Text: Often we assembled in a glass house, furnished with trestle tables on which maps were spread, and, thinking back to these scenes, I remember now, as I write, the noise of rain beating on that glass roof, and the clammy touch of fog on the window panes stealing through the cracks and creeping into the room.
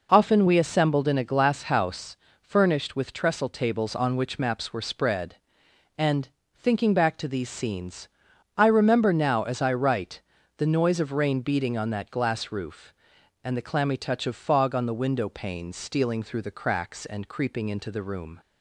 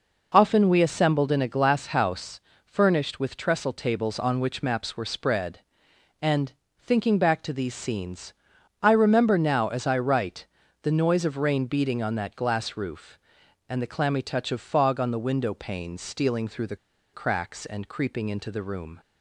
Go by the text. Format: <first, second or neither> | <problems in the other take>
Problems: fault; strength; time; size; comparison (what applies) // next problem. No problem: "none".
first | pauses between "the" and "cracks"; at 16.7 s; 0.37 s long